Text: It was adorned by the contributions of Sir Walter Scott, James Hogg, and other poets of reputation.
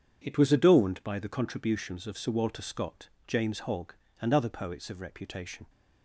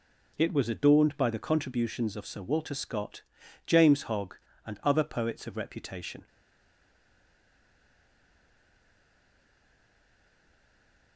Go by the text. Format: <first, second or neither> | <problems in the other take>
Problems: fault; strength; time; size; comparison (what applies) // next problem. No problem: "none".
first | stays silent after the last word; strong; from 6.2 s on; 4.9 s long